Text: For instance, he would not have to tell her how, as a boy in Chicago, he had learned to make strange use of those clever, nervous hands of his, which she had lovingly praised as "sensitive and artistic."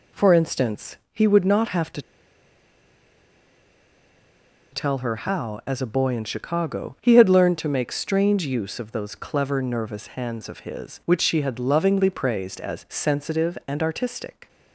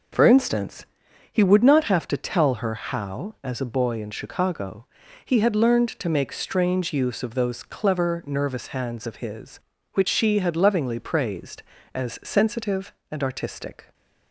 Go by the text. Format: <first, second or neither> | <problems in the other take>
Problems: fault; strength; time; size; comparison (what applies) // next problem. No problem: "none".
second | pauses between "to" and "tell"; strong; at 2.0 s; 2.7 s long